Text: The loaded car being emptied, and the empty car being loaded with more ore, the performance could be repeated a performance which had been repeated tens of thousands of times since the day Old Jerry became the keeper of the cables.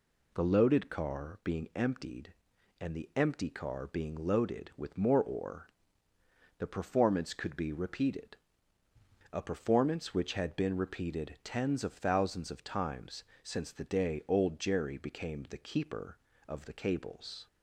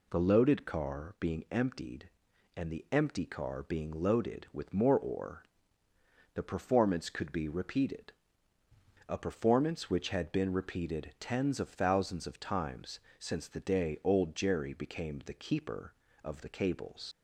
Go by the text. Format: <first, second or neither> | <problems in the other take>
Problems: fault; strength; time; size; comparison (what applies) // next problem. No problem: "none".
first | pauses between "repeated" and "a"; noticeable; at 8.1 s; 0.96 s long; noticeable in the first // pauses between "times" and "since"; slight; at 13.0 s; 0.18 s long; slight in the first // leaves "cables" unfinished; at 17.1 s; 115 ms